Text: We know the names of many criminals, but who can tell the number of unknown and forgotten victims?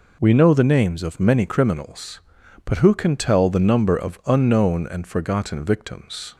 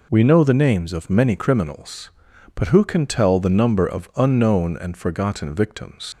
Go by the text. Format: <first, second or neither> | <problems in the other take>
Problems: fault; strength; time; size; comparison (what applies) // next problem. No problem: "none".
first | leaves "victims" unfinished; at 6.1 s; 130 ms